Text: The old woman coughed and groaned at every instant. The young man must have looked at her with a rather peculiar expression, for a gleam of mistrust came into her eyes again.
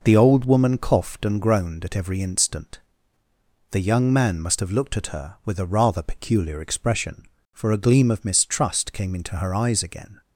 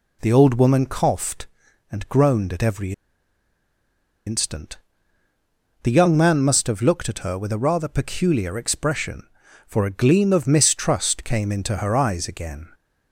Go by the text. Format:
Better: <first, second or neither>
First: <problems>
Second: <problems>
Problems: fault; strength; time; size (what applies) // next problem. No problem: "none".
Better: first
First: none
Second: pauses between "every" and "instant"; strong; at 2.9 s; 1.3 s long